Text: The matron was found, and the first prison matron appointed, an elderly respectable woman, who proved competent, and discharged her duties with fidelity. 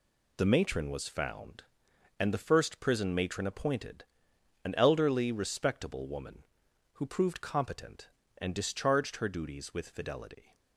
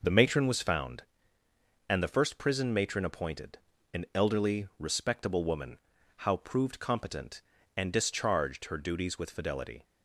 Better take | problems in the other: first | says "how" for "who"; at 6.1 s

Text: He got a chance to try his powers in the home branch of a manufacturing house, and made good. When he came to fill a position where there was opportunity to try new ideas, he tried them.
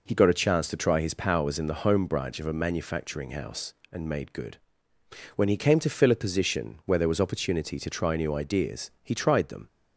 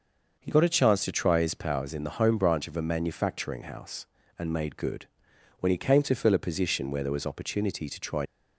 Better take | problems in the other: first | stops before "new ideas he tried them"; at 8.2 s

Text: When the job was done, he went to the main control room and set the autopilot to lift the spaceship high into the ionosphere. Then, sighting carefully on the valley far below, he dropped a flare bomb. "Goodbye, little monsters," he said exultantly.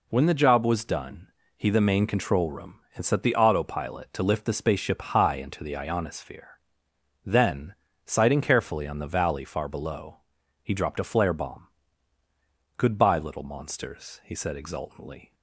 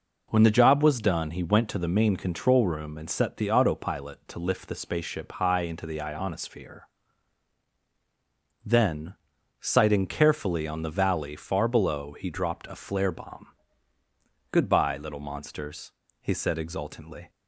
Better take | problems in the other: second | skips "went to"; at 1.6 s

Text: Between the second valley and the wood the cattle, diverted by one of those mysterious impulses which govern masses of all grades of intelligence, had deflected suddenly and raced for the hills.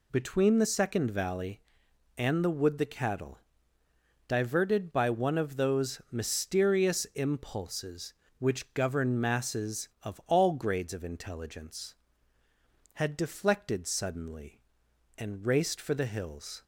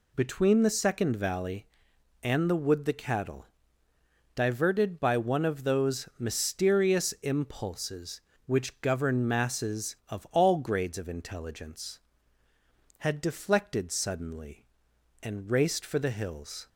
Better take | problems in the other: neither | none

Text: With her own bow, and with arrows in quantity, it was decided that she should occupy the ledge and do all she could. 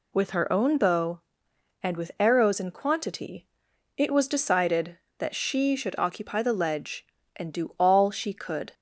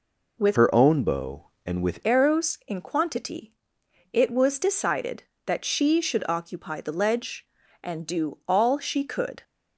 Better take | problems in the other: first | changes voice from "her" to "with"; from 0.5 to 2.0 s; 1.5 s long

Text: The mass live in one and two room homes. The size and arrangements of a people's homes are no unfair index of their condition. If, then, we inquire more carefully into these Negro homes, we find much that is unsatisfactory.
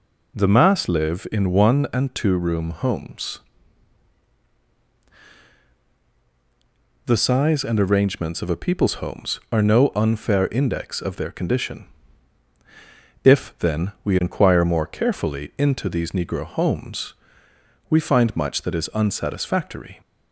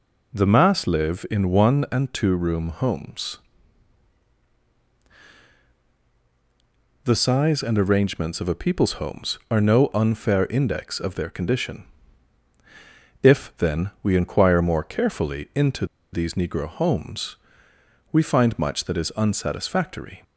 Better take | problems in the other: first | pauses between "into" and "these"; slight; at 15.8 s; 0.27 s long

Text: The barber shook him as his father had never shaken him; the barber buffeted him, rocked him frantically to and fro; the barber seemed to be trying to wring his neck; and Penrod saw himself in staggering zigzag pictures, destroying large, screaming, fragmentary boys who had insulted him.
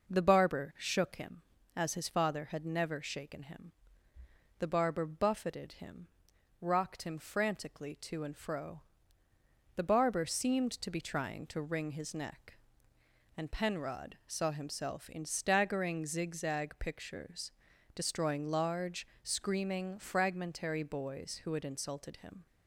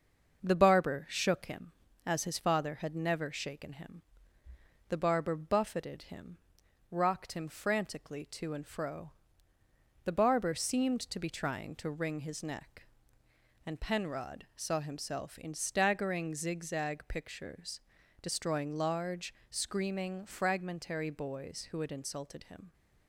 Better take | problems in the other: first | gets quieter; slight; throughout; 2 dB

